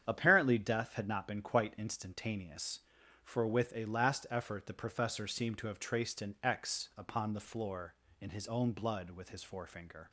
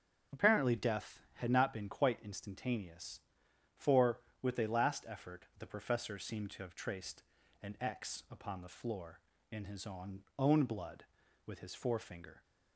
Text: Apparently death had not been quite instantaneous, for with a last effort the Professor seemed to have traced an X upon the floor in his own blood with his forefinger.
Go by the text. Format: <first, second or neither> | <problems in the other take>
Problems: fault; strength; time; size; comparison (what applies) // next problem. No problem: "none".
first | starts louder than the rest; strong; until 1.4 s; 8 dB; strong in the first // pauses between "traced" and "an"; at 7.2 s; 0.40 s long // says "own" twice; at 10.3 s